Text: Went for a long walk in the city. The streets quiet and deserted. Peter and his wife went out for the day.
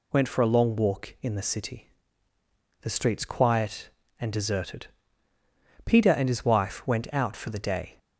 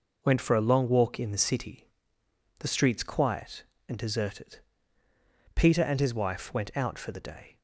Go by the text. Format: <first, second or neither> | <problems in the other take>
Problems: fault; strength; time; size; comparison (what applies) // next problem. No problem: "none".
neither | none